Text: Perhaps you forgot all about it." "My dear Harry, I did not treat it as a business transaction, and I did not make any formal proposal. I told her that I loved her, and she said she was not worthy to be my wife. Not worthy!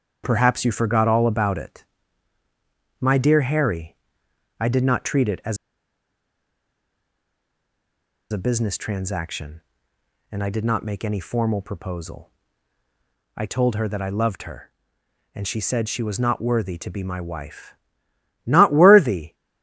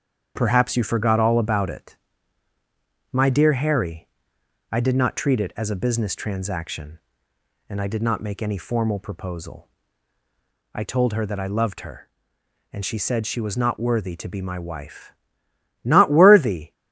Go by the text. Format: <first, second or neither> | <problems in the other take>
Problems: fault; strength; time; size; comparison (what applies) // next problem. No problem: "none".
second | starts louder than the rest; strong; until 1.2 s; 8 dB; strong in the second // pauses between "as" and "a"; strong; at 5.5 s; 2.7 s long